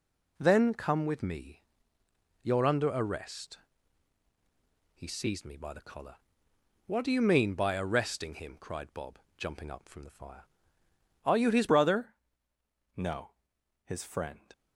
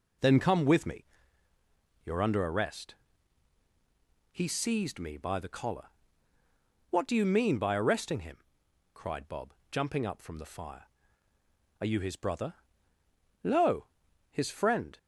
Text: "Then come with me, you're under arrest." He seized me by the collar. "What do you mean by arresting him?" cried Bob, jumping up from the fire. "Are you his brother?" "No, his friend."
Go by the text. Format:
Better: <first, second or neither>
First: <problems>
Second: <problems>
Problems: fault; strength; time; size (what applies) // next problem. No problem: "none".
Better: second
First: changes voice at "brother"; from 11.6 s on; 2.4 s long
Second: none